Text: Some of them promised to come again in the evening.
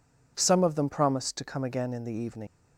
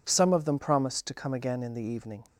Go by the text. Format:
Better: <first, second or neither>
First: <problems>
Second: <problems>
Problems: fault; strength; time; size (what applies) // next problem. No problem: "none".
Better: second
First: leaves "evening" unfinished; at 2.4 s; 95 ms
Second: none